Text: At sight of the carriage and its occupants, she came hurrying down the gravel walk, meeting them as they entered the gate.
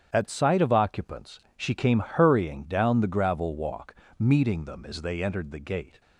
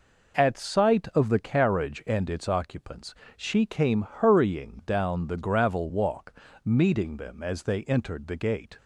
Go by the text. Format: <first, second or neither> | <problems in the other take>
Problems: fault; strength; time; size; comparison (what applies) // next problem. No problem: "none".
second | starts louder than the rest; strong; until 1.1 s; 9 dB // skips "the carriage and its"; at 0.7 s